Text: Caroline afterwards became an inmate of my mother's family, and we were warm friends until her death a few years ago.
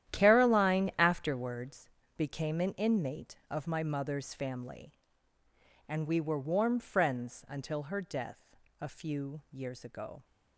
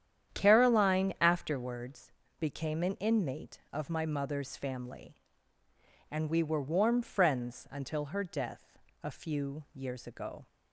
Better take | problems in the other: second | gets quieter; strong; throughout; 14 dB // starts louder than the rest; strong; until 1.2 s; 11.5 dB; strong in the second // pauses between "afterwards" and "became"; slight; at 1.8 s; 0.26 s long; slight in the second // pauses between "death" and "a"; slight; at 8.5 s; 0.24 s long; slight in the second

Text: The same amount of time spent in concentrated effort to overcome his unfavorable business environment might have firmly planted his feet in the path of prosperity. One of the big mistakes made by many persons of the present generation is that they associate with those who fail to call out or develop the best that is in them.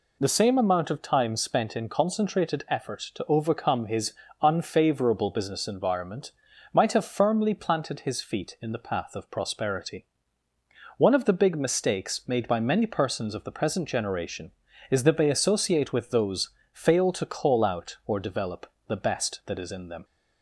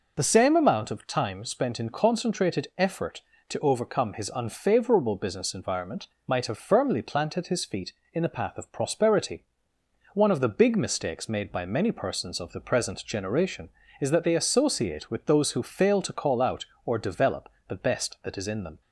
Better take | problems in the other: second | pauses between "his" and "unfavorable"; slight; at 4.1 s; 0.28 s long // pauses between "environment" and "might"; at 6.3 s; 0.42 s long; slight in the second // skips "who"; at 16.6 s // pauses between "develop" and "the"; slight; at 18.6 s; 0.20 s long; slight in the second

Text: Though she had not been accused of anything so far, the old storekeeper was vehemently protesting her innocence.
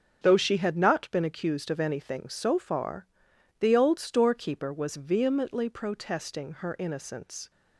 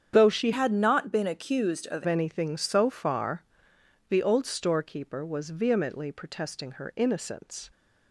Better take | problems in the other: first | starts louder than the rest; strong; until 1.1 s; 8 dB; also in the first // changes voice from "had" to "of"; from 0.5 to 2.0 s; 1.5 s long

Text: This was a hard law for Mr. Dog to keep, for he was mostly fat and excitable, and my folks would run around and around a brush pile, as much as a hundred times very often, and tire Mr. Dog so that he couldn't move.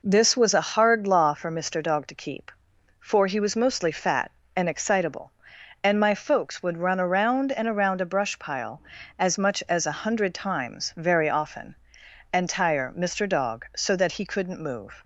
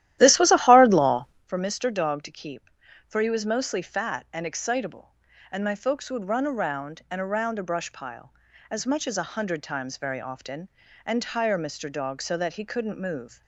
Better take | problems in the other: first | starts louder than the rest; strong; until 1.5 s; 13.5 dB

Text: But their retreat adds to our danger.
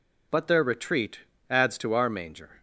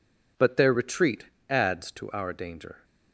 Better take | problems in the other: second | pauses between "retreat" and "adds"; slight; at 1.2 s; 0.28 s long; slight in the second // says "manger" for "danger"; at 2.0 s

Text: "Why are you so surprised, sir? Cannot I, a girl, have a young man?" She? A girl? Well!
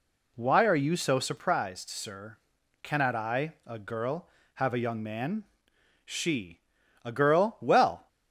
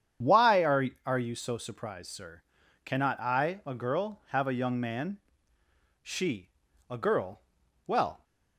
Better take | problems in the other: first | starts louder than the rest; strong; until 1.4 s; 8 dB // says "are" twice; at 1.0 s

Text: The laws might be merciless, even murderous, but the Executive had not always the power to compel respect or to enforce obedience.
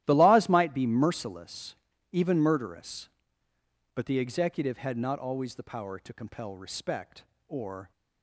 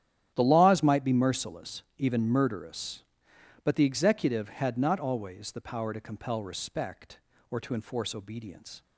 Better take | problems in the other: second | starts louder than the rest; strong; until 1.0 s; 13.5 dB; strong in the second // stops before "to enforce obedience"; at 7.9 s

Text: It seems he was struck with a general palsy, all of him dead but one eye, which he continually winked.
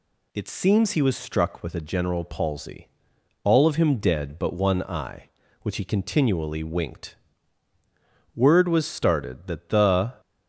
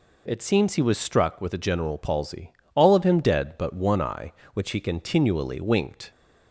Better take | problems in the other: second | goes on to say "Word was started that the"; strong; from 8.3 s on; 1.8 s long

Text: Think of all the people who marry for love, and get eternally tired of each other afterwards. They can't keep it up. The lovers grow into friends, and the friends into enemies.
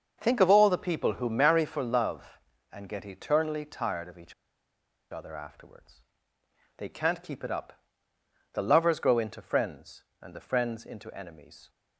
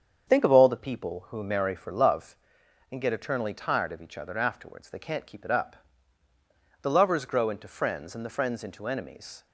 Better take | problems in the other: second | starts louder than the rest; until 1.2 s; 6.5 dB; strong in the second // pauses between "each" and "other"; noticeable; at 4.3 s; 0.77 s long

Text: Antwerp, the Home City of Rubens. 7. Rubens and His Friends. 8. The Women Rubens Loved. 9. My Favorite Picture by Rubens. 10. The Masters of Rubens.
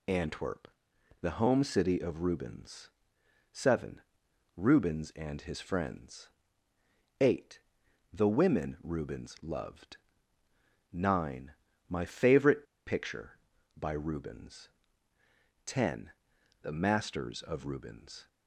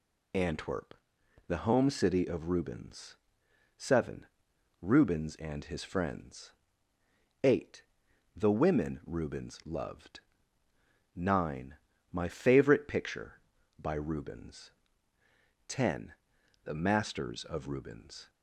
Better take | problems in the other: second | pauses between "Favorite" and "Picture"; slight; at 12.6 s; 0.22 s long

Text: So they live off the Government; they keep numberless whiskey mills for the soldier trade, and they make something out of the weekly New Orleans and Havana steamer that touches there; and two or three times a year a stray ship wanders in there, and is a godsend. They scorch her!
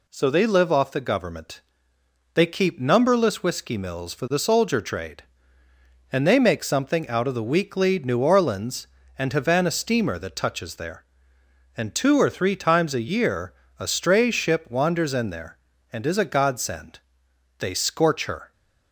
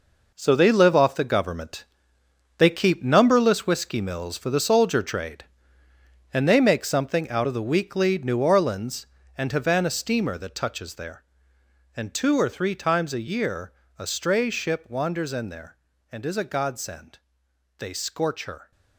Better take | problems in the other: first | gets quieter; strong; throughout; 10 dB // pauses between "year" and "a"; slight; at 13.7 s; 0.24 s long; slight in the first

